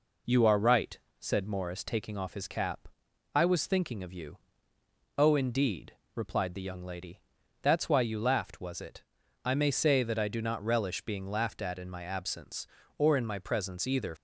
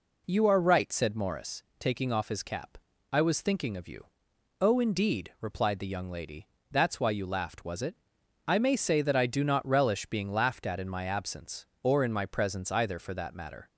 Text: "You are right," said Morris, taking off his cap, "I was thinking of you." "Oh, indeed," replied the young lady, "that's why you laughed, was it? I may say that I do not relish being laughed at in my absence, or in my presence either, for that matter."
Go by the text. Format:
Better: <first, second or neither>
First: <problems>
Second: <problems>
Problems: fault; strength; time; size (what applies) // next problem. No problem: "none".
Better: second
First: stops before "for that matter"; at 14.1 s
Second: none